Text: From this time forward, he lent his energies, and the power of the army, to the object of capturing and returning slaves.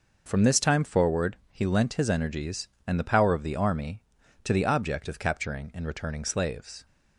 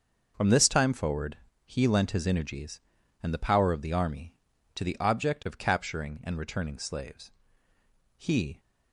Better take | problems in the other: first | starts louder than the rest; until 1.3 s; 6.5 dB // goes on to say "He"; slight; from 8.1 s on; 0.42 s long

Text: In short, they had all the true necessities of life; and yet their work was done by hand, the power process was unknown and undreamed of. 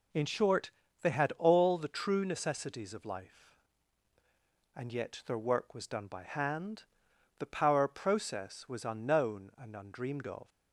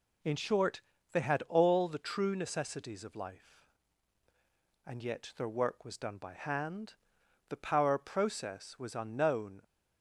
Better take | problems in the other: first | stops before "and undreamed of"; at 9.6 s

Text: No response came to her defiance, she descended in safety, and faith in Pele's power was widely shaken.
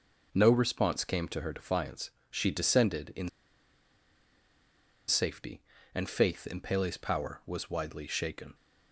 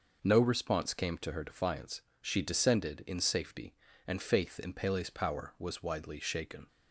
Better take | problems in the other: second | pauses between "in" and "safety"; strong; at 3.2 s; 1.7 s long

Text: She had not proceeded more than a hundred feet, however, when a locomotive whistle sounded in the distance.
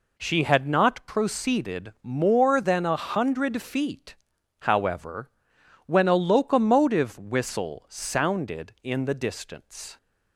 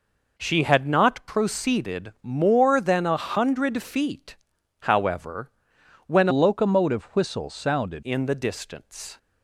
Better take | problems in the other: first | changes voice from "locomotive" to "sounded"; from 6.3 to 8.0 s; 1.7 s long

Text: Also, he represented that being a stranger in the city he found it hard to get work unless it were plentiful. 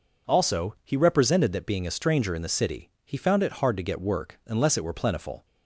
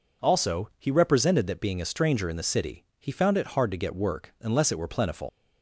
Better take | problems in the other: first | pauses between "city" and "he"; slight; at 2.8 s; 0.16 s long; slight in the first // leaves "plentiful" unfinished; at 5.2 s; 100 ms

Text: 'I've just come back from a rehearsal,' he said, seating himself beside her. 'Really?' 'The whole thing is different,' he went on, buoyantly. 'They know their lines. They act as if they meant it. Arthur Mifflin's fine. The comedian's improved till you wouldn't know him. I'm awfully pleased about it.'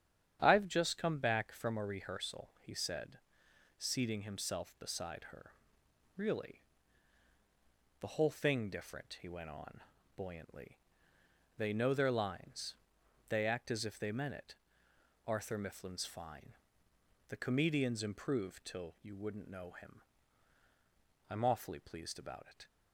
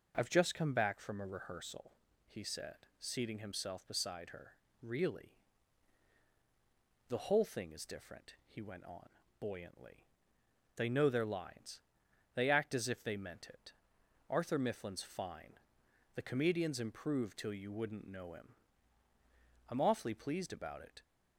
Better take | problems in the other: second | starts louder than the rest; strong; until 1.4 s; 9 dB // skips "is"; at 8.7 s

